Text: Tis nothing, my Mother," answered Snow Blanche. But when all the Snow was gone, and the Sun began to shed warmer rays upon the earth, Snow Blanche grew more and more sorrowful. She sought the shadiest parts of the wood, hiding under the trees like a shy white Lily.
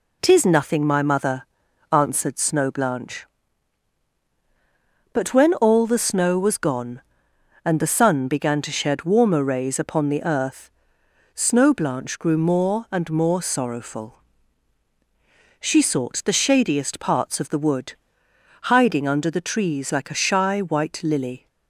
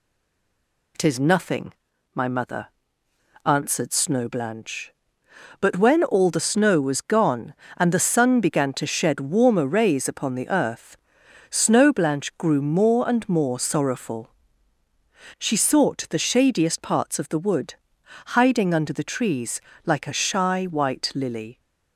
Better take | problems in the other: first | stays silent before the first word; slight; until 0.9 s; 0.9 s long // pauses between "trees" and "like"; slight; at 19.5 s; 0.24 s long

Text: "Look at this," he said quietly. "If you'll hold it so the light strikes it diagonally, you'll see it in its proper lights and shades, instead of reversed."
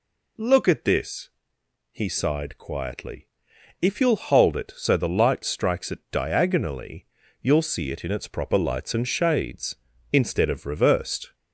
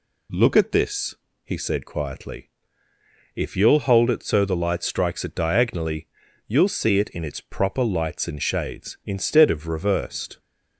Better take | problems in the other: second | says "sighed" for "said"; at 2.0 s

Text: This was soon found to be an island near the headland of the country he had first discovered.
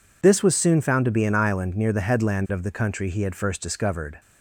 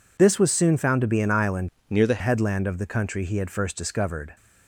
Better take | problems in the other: first | changes voice from "near" to "the"; from 1.8 to 2.2 s; 0.4 s long

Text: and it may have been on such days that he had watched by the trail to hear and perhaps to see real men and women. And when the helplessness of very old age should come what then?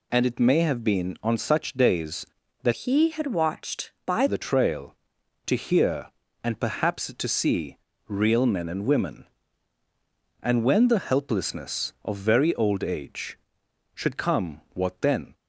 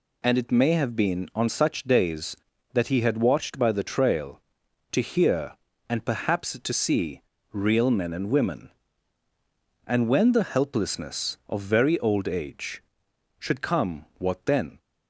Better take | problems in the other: second | changes voice from "he" to "by"; from 2.7 to 4.2 s; 1.5 s long // pauses between "see" and "real"; slight; at 7.7 s; 0.30 s long; slight in the second

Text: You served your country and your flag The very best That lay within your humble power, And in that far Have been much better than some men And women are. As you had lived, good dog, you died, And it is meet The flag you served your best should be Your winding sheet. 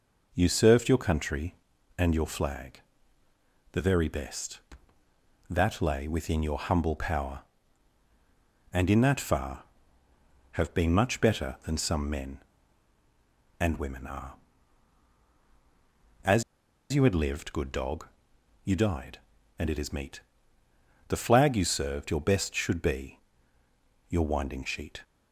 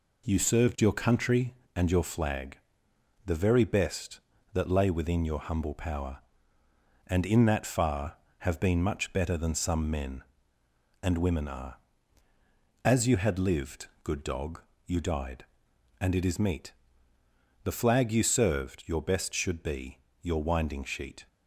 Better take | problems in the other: second | pauses between "flag" and "The"; noticeable; at 2.8 s; 0.90 s long; noticeable in the second // pauses between "As" and "you"; noticeable; at 16.4 s; 0.50 s long // pauses between "meet" and "The"; noticeable; at 20.2 s; 0.86 s long; noticeable in the second // pauses between "be" and "Your"; noticeable; at 23.1 s; 0.90 s long; slight in the second

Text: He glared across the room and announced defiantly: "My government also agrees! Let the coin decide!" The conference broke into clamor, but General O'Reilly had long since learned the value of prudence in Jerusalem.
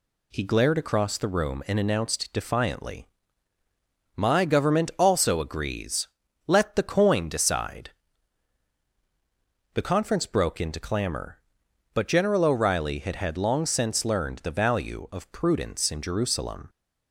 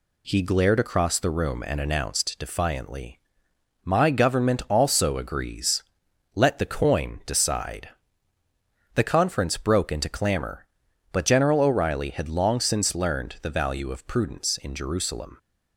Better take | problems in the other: second | says "had" twice; at 13.1 s

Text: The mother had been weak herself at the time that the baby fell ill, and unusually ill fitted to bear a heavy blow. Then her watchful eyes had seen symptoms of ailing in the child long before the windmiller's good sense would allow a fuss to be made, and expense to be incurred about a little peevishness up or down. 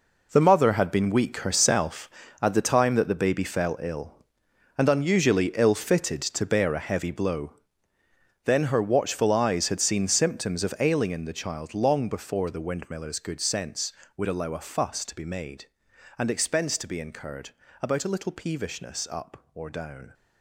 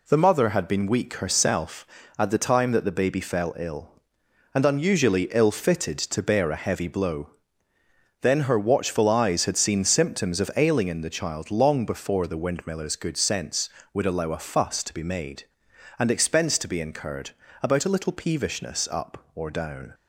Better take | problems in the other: second | gets quieter; strong; throughout; 11.5 dB // pauses between "incurred" and "about"; slight; at 17.5 s; 0.30 s long; slight in the second

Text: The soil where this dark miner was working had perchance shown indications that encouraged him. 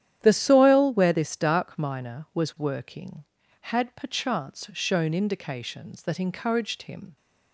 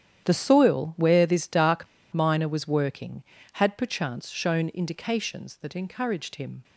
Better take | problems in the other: first | starts louder than the rest; strong; until 1.2 s; 10 dB; strong in the first // pauses between "dark" and "miner"; slight; at 1.8 s; 0.26 s long

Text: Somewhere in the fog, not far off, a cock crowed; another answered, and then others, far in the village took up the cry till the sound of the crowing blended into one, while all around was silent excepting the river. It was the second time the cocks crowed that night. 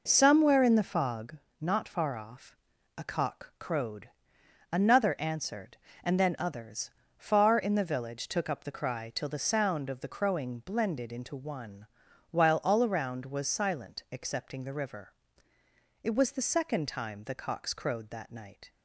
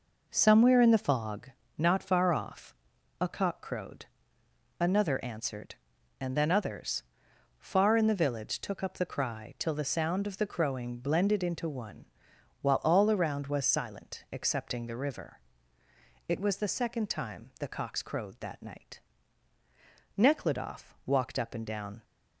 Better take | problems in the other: first | goes on to say "Nekhludoff walked up and down"; strong; from 20.1 s on; 1.8 s long

